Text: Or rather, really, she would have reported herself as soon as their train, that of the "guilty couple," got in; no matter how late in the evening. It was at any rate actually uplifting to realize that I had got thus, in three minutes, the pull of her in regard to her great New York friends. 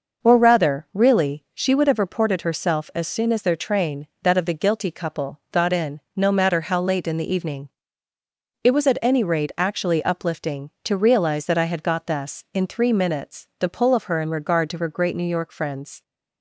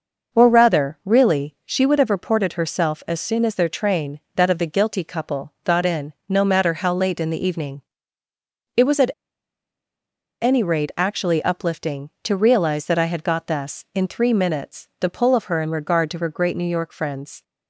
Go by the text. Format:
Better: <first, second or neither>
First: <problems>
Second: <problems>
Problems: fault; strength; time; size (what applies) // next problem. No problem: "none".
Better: first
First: none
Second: pauses between "at" and "any"; strong; at 9.0 s; 1.3 s long